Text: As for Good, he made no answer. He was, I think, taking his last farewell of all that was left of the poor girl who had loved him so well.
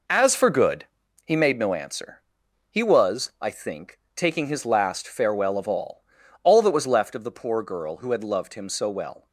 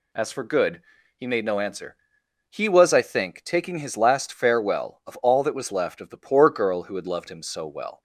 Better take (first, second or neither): second